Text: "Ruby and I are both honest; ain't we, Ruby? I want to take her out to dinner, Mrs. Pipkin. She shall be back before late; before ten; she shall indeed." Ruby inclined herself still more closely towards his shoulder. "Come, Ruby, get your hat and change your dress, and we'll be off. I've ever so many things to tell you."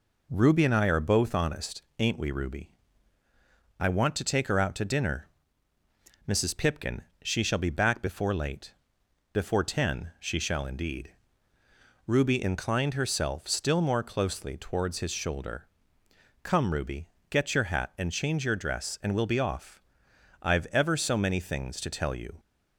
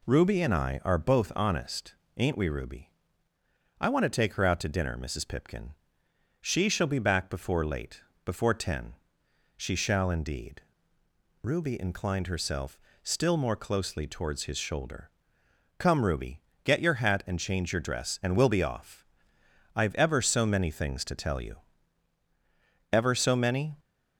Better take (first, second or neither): first